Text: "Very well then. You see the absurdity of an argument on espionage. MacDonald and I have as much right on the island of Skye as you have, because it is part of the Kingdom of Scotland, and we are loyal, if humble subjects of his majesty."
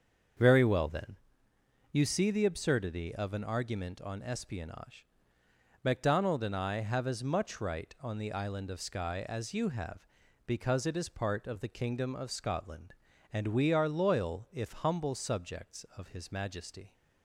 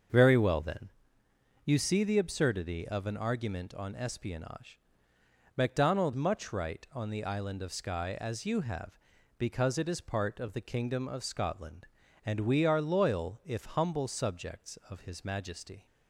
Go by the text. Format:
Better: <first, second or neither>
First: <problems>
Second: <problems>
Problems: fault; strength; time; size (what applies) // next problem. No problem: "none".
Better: first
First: starts louder than the rest; until 2.1 s; 7 dB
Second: starts louder than the rest; until 1.8 s; 7 dB // skips "and I have as"; at 6.1 s